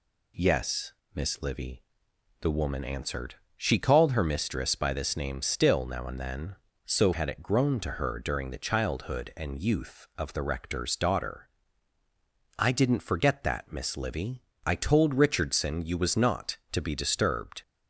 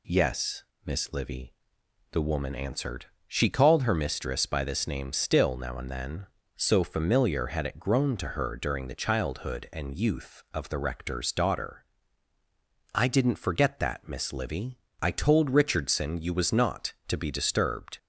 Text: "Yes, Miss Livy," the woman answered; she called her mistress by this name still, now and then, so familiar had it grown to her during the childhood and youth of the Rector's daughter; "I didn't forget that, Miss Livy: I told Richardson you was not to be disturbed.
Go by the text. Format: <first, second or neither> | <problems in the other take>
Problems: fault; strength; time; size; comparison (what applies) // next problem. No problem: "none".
second | skips "familiar"; at 7.1 s